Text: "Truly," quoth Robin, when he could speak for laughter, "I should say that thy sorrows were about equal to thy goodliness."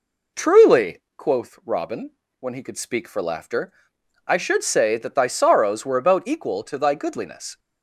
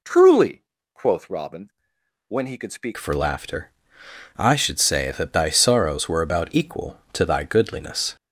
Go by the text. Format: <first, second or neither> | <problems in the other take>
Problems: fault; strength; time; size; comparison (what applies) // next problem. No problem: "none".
first | changes voice at "for"; from 2.9 s on; 5.2 s long